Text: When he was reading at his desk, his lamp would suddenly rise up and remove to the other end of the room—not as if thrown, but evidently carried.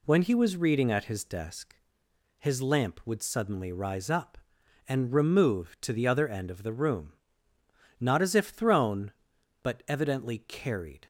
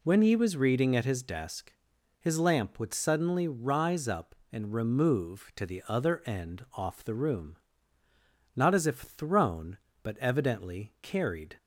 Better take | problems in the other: first | says "off" for "of"; at 6.7 s

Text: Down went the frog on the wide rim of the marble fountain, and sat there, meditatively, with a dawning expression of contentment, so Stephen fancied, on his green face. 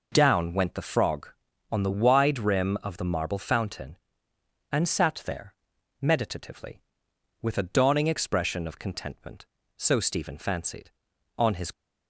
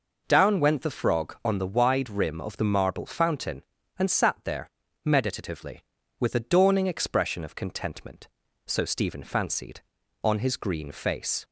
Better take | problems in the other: second | stops before "green face"; at 11.7 s

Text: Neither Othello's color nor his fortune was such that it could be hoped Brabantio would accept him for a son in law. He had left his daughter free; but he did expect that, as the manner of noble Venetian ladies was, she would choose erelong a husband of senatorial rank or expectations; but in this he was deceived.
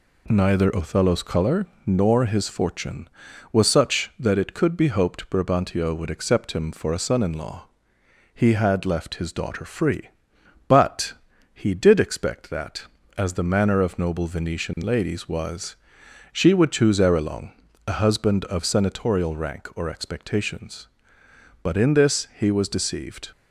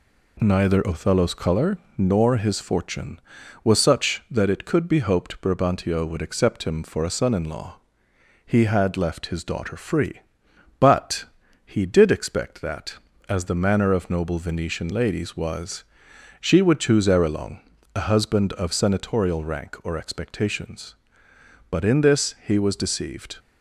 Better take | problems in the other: neither | pauses between "color" and "nor"; slight; the same in both // pauses between "but" and "he"; the same in both // pauses between "erelong" and "a"; slight; the same in both

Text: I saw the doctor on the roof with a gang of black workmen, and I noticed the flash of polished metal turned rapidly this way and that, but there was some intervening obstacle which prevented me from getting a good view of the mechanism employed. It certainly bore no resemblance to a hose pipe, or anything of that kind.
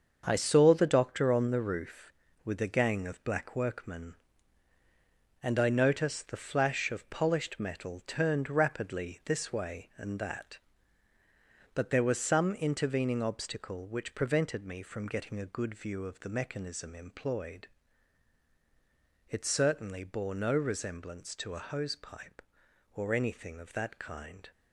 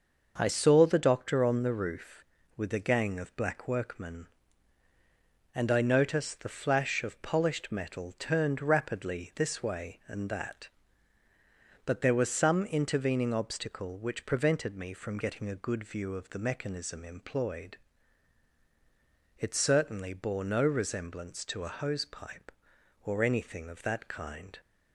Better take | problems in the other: second | gets quieter; strong; throughout; 8.5 dB // starts louder than the rest; until 1.2 s; 7 dB; also in the second

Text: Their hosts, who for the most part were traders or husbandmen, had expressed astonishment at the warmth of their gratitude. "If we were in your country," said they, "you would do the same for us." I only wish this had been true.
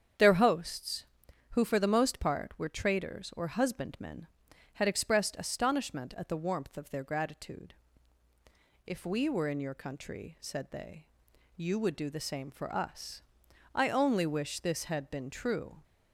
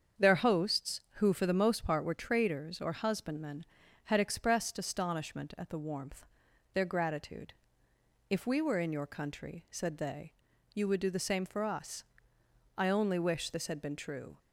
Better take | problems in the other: first | starts louder than the rest; strong; until 1.3 s; 7.5 dB; strong in the first // skips "of"; at 6.4 s

